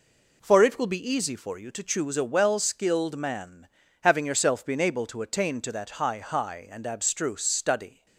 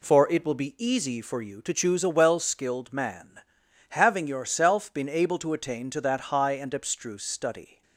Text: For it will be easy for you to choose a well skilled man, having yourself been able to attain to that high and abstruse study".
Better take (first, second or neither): second